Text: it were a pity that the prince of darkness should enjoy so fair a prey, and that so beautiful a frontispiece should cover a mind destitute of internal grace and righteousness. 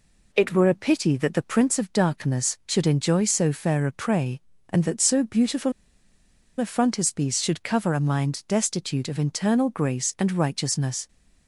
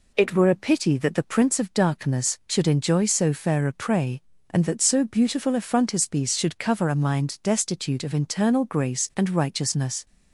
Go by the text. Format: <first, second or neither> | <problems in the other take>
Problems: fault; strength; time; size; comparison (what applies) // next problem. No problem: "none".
second | pauses between "beautiful" and "a"; noticeable; at 5.7 s; 0.87 s long